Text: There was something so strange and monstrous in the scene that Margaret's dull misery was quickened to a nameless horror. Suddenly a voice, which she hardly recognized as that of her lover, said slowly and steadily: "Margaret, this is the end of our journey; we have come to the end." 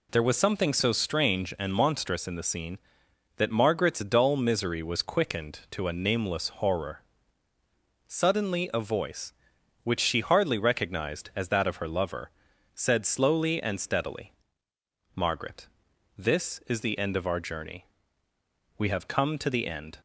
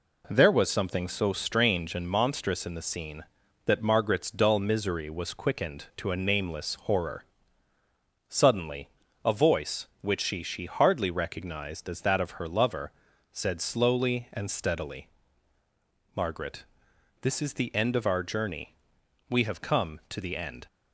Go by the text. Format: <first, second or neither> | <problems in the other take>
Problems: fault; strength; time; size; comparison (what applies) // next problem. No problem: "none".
first | pauses between "Suddenly" and "a"; slight; at 8.8 s; 0.34 s long // says "she" twice; at 10.4 s